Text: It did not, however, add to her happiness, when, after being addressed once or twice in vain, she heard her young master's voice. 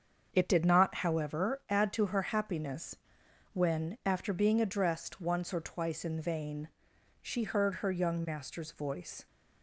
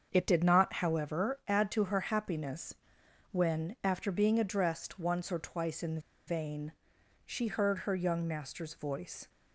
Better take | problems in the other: first | starts louder than the rest; until 1.1 s; 7 dB; also in the first // pauses between "in" and "vain"; slight; at 5.9 s; 0.28 s long

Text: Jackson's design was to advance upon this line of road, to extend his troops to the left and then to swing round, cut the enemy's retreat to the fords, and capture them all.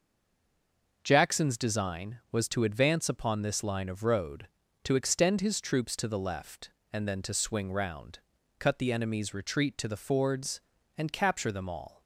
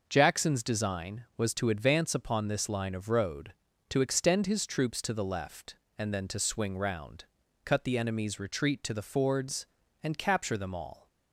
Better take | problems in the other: second | stays silent before the first word; until 1.0 s; 1.0 s long

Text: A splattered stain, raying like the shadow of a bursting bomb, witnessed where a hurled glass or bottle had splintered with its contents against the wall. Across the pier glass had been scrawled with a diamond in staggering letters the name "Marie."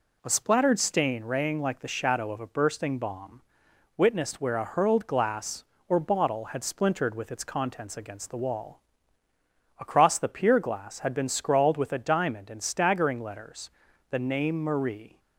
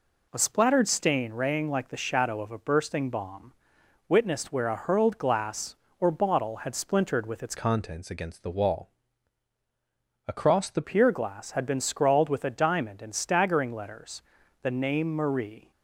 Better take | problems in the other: first | changes voice from "contents" to "the"; from 7.5 to 10.8 s; 3.3 s long // pauses between "letters" and "the"; at 14.2 s; 0.40 s long; also in the first

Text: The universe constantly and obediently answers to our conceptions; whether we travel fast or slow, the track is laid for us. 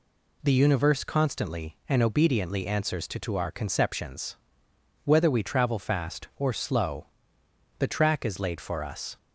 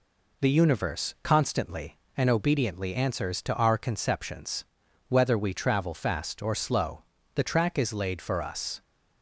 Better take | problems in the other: second | says "to" twice; at 3.1 s

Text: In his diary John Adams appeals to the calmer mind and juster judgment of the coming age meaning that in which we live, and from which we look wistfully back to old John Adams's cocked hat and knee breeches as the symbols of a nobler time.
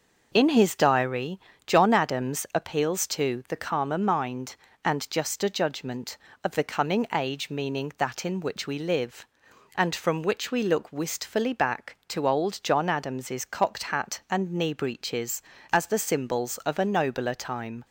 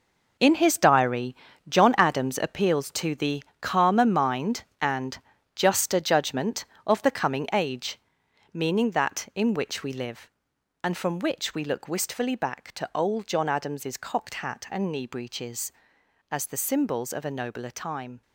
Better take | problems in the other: first | gets quieter; strong; throughout; 11.5 dB // pauses between "diary" and "John"; slight; at 1.3 s; 0.36 s long; slight in the first // pauses between "the" and "calmer"; slight; at 3.4 s; 0.20 s long // pauses between "and" and "juster"; at 5.1 s; 0.38 s long // pauses between "age" and "meaning"; noticeable; at 7.9 s; 0.54 s long

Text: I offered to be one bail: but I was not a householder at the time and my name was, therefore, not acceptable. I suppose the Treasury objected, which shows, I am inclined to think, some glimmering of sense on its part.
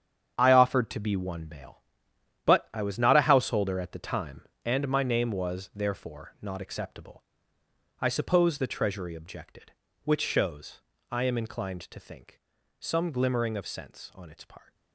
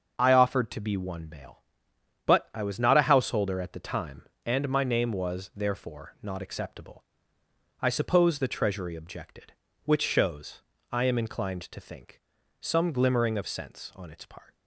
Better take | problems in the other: second | gets quieter; strong; throughout; 10.5 dB // starts louder than the rest; strong; until 1.3 s; 8 dB; noticeable in the second

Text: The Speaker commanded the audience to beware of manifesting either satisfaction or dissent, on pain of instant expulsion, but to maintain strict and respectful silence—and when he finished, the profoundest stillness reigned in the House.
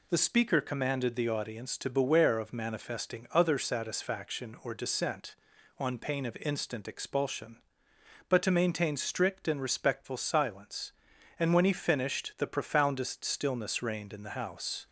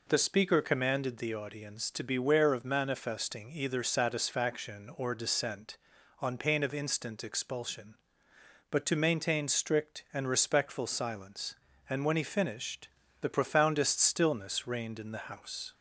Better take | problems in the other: second | says "other" for "either"; at 3.3 s

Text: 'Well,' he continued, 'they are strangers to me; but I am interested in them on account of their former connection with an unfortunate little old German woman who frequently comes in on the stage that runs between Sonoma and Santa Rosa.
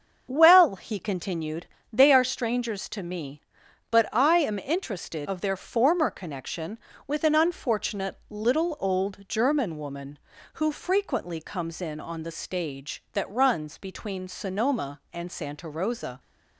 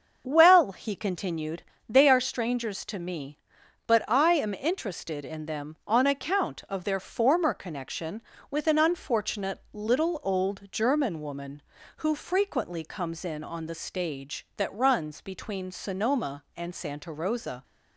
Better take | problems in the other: second | starts louder than the rest; until 1.3 s; 7 dB; also in the second // skips "in them on account"; at 5.2 s

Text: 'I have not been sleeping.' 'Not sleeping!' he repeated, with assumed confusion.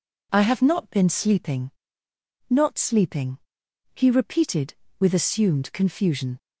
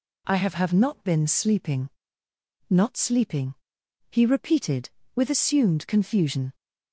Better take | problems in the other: first | says "have" twice; at 0.5 s

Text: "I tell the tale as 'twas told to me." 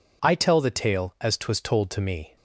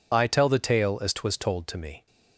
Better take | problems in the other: first | loses the start of "I"; at 0.1 s; 45 ms

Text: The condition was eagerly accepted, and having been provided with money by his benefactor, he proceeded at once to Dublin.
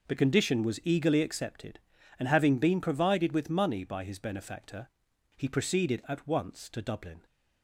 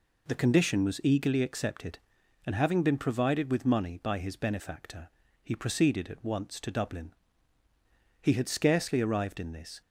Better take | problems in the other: first | goes on to say "He had scarcely arrived in this"; from 8.2 s on; 1.6 s long

